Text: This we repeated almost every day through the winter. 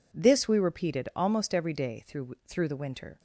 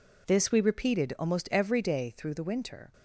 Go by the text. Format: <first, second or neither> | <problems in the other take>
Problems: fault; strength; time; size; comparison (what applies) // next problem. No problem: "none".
second | says "through" twice; at 2.4 s